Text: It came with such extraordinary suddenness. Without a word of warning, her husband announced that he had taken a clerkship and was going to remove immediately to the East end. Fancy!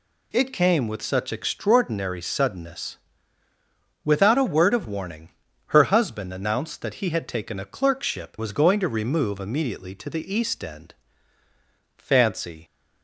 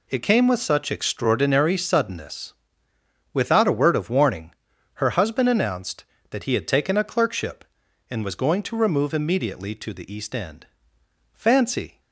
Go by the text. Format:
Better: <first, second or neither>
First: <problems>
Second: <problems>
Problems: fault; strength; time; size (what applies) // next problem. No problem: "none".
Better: second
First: skips "and"; at 8.3 s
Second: none